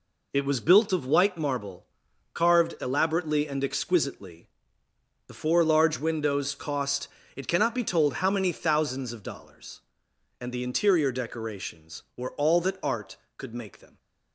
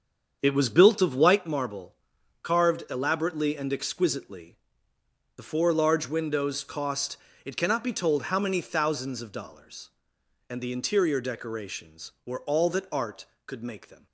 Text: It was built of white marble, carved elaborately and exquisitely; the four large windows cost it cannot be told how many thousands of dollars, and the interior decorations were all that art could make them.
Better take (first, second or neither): first